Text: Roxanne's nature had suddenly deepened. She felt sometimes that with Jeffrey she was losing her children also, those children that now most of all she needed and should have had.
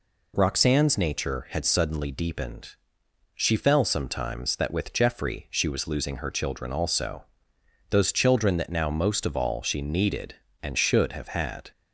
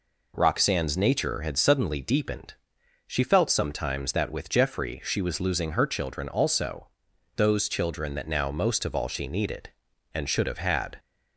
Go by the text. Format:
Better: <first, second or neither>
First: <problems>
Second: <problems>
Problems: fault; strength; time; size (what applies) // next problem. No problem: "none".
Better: second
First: says "fell" for "felt"; at 3.5 s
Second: none